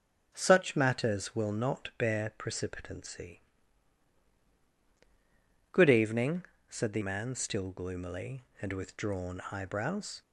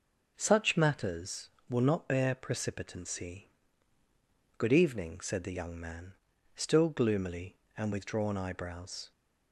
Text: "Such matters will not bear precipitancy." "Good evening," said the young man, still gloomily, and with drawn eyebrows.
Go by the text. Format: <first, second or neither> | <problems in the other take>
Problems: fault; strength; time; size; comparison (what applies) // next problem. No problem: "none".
second | skips "young"; at 7.0 s